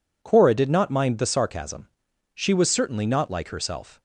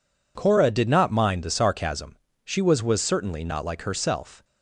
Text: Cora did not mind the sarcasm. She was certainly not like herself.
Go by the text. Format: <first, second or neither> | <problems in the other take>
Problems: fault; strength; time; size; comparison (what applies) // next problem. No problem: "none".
first | says "was" twice; at 2.8 s